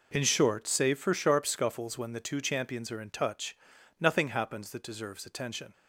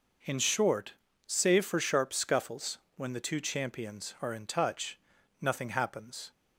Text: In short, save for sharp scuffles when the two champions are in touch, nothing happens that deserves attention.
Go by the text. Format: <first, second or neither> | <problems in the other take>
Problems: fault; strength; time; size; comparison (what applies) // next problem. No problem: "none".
first | pauses between "scuffles" and "when"; slight; at 2.7 s; 0.20 s long // stops before "that deserves attention"; at 6.3 s